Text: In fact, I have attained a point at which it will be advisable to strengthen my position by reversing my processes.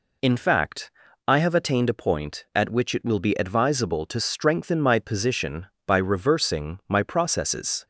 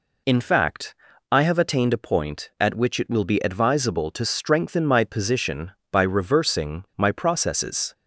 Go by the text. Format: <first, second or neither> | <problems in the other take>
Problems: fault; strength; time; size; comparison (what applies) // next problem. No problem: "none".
neither | none